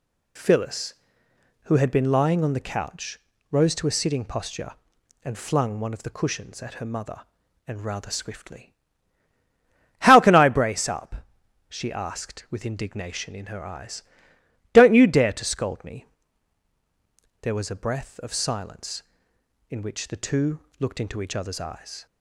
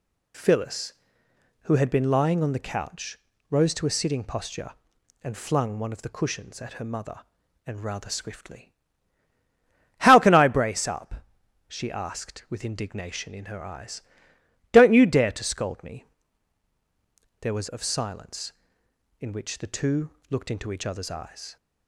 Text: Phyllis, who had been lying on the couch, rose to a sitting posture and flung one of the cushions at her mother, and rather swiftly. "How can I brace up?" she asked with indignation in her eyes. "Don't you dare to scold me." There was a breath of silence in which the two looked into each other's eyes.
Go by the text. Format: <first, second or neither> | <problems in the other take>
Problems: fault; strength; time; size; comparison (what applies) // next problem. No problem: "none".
first | skips "a breath"; at 17.6 s // pauses between "two" and "looked"; slight; at 20.1 s; 0.18 s long; slight in the first